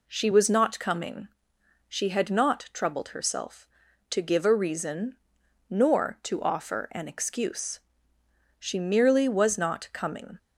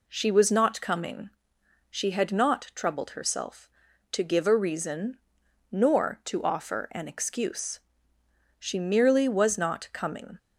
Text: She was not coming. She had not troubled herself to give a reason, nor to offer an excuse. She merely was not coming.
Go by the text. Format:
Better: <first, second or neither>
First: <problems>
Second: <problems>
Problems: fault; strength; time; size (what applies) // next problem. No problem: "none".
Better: neither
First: none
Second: none